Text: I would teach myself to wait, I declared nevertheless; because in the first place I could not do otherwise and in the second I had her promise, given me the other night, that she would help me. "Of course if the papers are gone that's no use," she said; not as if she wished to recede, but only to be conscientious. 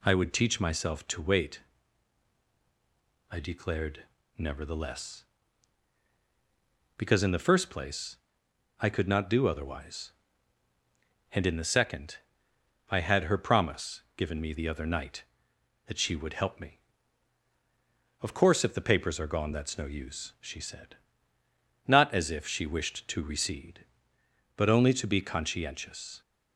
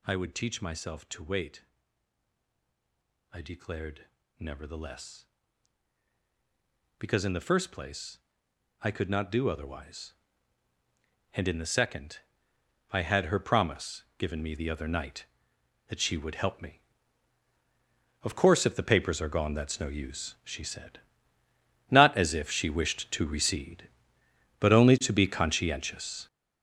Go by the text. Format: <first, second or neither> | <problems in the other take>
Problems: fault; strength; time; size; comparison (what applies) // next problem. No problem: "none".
first | gets louder; strong; throughout; 10.5 dB // pauses between "declared" and "nevertheless"; slight; at 4.0 s; 0.30 s long; slight in the first // pauses between "place" and "I"; noticeable; at 8.1 s; 0.62 s long; noticeable in the first // pauses between "second" and "I"; noticeable; at 12.1 s; 0.72 s long; noticeable in the first